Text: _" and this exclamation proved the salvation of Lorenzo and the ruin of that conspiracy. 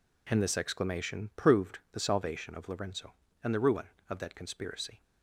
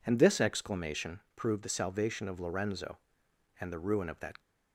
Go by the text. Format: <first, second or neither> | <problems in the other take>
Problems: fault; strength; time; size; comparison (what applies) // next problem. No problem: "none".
first | pauses between "exclamation" and "proved"; slight; at 1.1 s; 0.16 s long // stops before "conspiracy"; at 4.3 s